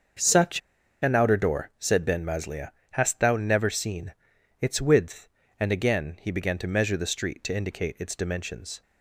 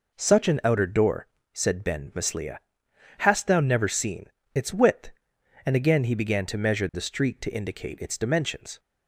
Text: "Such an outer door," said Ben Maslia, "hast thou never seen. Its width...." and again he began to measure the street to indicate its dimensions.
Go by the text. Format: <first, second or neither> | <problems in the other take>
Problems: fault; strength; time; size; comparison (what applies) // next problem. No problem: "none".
second | starts louder than the rest; until 1.6 s; 6.5 dB // pauses between "Such" and "an"; at 0.6 s; 0.43 s long